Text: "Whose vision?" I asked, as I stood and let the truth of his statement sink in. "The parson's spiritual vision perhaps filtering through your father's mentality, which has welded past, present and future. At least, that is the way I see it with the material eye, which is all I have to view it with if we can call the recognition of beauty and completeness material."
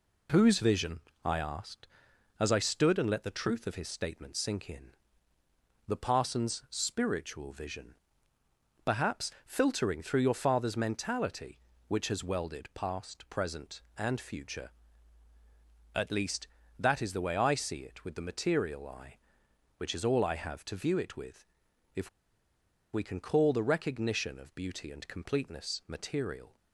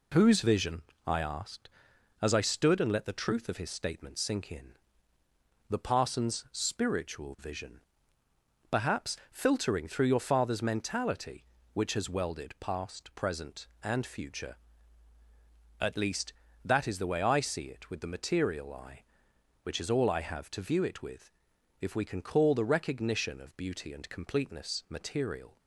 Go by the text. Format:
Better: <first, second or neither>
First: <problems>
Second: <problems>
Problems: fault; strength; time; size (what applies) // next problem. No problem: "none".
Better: second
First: pauses between "vision" and "perhaps"; noticeable; at 7.9 s; 0.88 s long // pauses between "with" and "if"; noticeable; at 21.4 s; 0.52 s long // pauses between "if" and "we"; noticeable; at 22.0 s; 0.84 s long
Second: pauses between "vision" and "perhaps"; noticeable; at 7.8 s; 0.88 s long // pauses between "with" and "if"; noticeable; at 21.3 s; 0.52 s long